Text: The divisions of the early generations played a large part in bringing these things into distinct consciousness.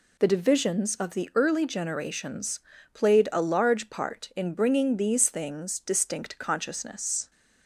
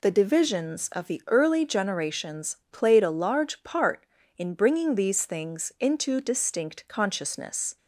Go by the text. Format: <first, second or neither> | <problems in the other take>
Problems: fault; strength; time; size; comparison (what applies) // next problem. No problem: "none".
second | pauses between "generations" and "played"; slight; at 2.5 s; 0.34 s long; slight in the second // skips "into"; at 5.8 s